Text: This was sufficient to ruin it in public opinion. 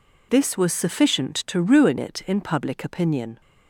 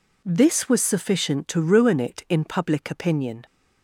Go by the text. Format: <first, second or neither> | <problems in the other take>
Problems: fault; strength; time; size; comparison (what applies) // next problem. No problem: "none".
neither | none